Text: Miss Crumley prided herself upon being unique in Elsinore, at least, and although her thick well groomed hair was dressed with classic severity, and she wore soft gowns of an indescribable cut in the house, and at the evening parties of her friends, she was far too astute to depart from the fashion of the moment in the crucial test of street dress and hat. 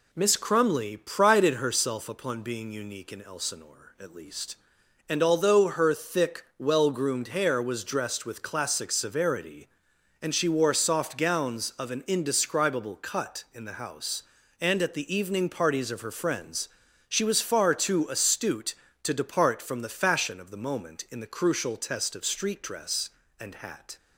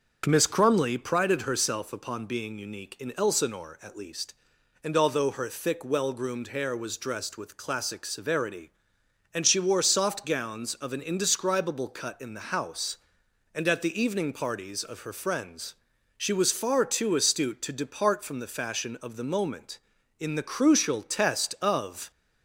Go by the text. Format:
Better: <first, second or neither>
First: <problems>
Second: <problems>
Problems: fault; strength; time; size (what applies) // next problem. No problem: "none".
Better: first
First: none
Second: stops before "street dress and hat"; at 22.1 s